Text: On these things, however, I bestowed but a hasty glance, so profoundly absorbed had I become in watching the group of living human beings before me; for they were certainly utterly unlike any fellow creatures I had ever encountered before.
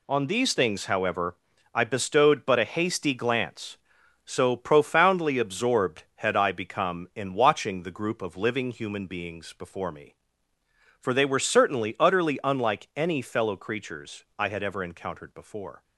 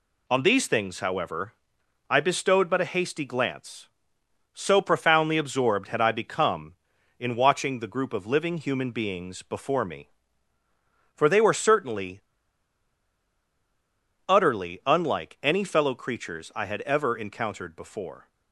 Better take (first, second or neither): first